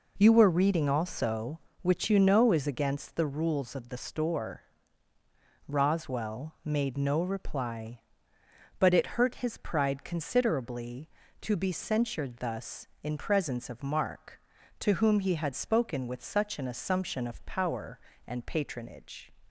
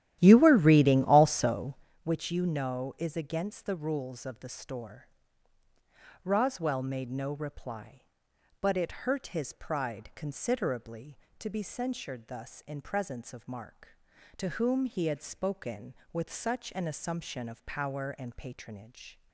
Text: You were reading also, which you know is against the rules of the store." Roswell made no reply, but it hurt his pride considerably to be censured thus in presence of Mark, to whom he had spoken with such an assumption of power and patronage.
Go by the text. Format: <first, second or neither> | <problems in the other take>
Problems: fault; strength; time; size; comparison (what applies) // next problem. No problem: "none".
first | starts louder than the rest; strong; until 1.9 s; 12.5 dB